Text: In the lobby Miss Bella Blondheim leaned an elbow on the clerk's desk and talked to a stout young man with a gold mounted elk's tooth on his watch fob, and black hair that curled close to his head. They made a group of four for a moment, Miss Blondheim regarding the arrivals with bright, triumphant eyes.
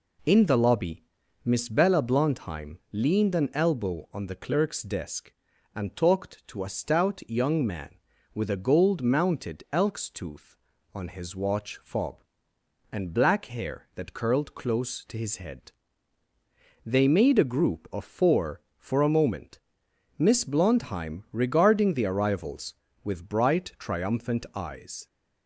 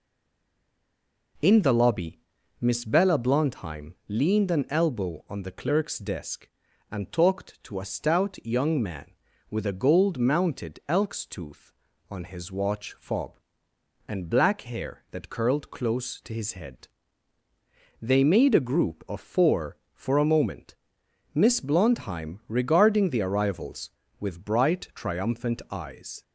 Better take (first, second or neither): first